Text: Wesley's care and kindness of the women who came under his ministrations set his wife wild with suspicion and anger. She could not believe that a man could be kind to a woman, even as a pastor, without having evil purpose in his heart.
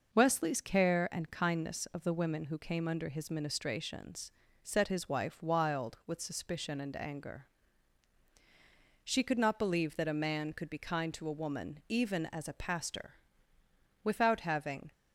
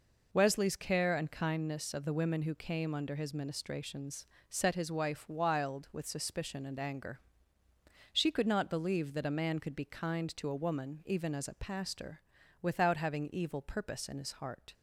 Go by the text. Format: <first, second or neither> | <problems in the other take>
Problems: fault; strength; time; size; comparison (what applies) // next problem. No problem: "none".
second | pauses between "ministrations" and "set"; slight; at 4.3 s; 0.28 s long; slight in the second // stops before "evil purpose in his heart"; at 14.9 s